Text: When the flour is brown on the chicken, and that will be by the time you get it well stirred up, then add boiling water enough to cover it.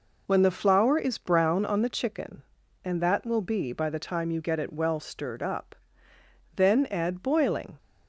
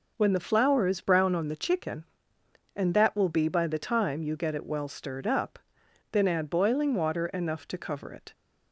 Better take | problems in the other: second | stops before "water enough to cover it"; at 7.7 s

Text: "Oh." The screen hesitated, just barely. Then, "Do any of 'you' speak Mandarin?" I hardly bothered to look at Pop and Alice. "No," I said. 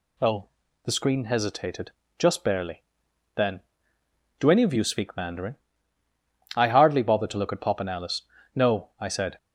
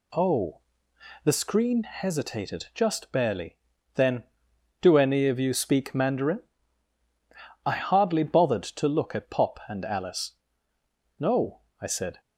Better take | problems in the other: neither | none

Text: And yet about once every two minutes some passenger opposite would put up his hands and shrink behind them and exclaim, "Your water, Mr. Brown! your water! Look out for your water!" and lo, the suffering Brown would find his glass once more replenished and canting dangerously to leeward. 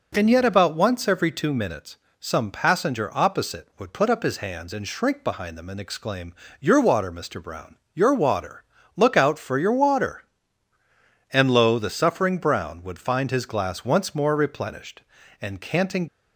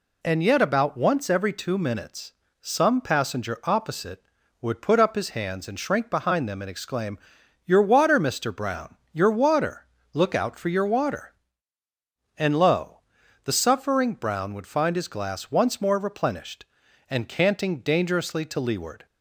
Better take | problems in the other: second | pauses between "minutes" and "some"; slight; at 1.9 s; 0.24 s long; slight in the second // stops before "dangerously to leeward"; at 16.0 s

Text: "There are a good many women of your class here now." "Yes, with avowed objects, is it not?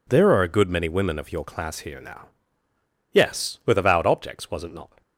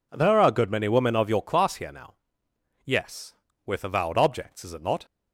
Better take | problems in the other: second | says "was" for "is"; at 4.4 s

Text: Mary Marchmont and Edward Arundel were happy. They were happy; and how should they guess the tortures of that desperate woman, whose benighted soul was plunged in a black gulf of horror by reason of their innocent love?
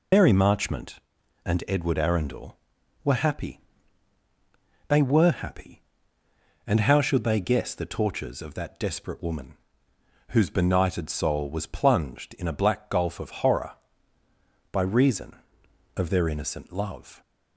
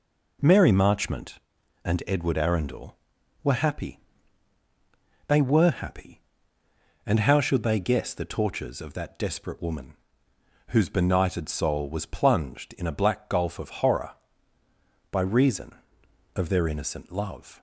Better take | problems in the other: second | loses the start of "Mary"; at 0.1 s; 125 ms

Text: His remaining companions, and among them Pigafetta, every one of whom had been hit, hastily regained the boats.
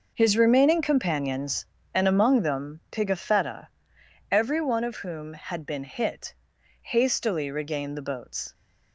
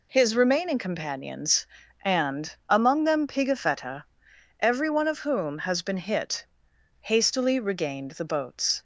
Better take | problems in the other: first | pauses between "and" and "among"; slight; at 2.5 s; 0.16 s long // says "has" for "had"; at 5.5 s

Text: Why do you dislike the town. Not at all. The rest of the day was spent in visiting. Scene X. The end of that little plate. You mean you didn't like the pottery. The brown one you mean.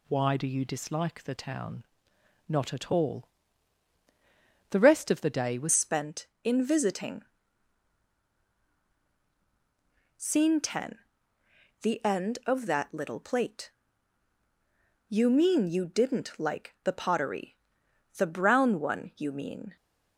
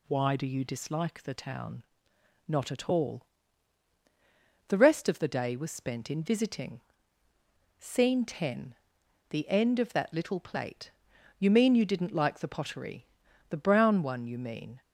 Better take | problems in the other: second | changes voice at "spent"; from 5.7 s on; 14.0 s long

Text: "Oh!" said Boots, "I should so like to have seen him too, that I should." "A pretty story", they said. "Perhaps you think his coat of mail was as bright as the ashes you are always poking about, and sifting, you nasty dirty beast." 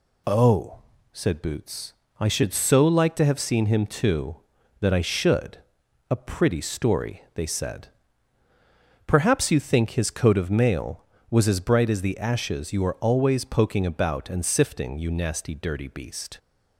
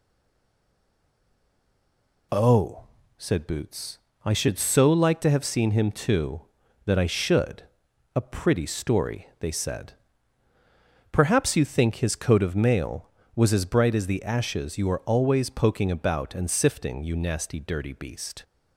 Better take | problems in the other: first | stays silent before the first word; until 2.3 s; 2.3 s long

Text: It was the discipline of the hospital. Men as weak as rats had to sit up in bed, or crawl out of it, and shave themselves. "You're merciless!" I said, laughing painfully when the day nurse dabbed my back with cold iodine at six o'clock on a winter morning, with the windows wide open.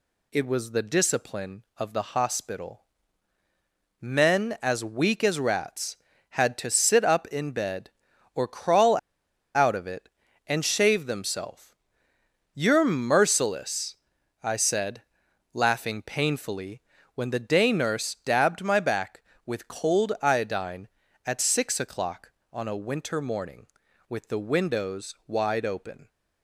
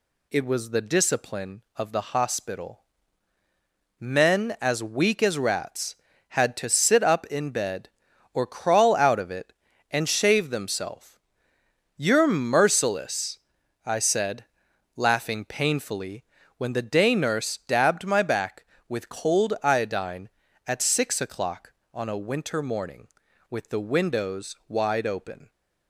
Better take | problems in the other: second | pauses between "crawl" and "out"; noticeable; at 8.9 s; 0.59 s long // pauses between "painfully" and "when"; slight; at 16.8 s; 0.32 s long; slight in the second

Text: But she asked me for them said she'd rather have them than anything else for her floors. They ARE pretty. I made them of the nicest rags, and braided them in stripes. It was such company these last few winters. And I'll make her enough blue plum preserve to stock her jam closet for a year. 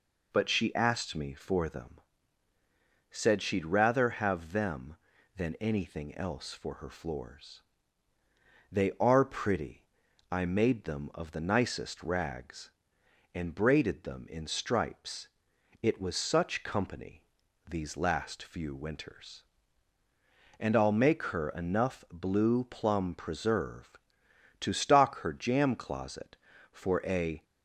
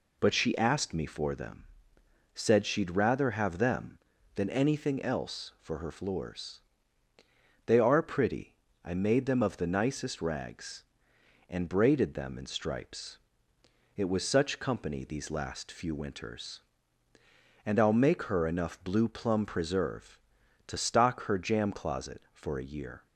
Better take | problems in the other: second | pauses between "them" and "said"; at 1.9 s; 1.1 s long; noticeable in the second // pauses between "company" and "these"; noticeable; at 17.2 s; 0.46 s long // stops before "year"; at 27.4 s

